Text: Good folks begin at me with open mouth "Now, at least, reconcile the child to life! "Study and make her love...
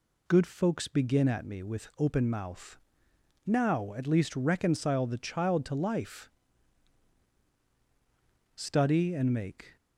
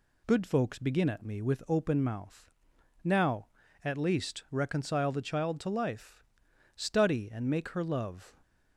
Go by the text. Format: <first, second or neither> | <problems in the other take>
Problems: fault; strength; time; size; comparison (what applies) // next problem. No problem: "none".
second | pauses between "mouth" and "Now"; noticeable; at 2.7 s; 0.66 s long; noticeable in the second // stops before "her love"; at 9.7 s